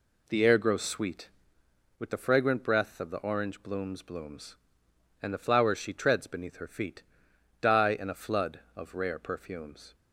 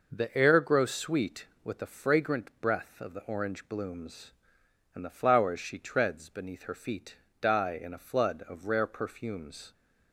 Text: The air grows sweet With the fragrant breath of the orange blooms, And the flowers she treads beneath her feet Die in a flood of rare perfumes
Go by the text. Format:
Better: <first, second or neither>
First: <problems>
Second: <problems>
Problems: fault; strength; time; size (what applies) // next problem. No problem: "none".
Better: second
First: says "blooms" twice; at 4.0 s // pauses between "feet" and "Die"; noticeable; at 7.0 s; 0.58 s long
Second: pauses between "feet" and "Die"; slight; at 7.1 s; 0.24 s long